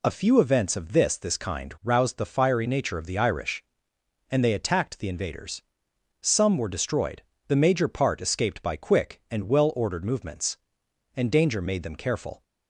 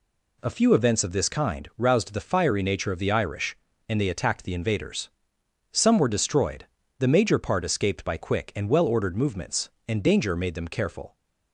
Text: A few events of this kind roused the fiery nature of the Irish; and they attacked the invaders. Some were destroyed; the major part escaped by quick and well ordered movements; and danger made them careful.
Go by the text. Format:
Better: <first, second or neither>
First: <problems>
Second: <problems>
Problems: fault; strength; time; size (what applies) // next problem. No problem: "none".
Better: second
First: says "this" twice; at 1.1 s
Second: none